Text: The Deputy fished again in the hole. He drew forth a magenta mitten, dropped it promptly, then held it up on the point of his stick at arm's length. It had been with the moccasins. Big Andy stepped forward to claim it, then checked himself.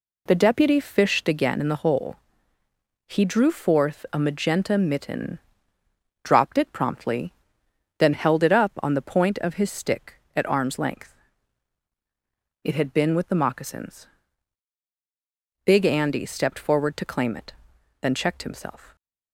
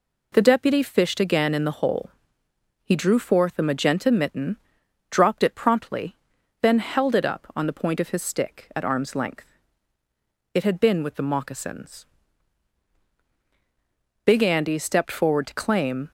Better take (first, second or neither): first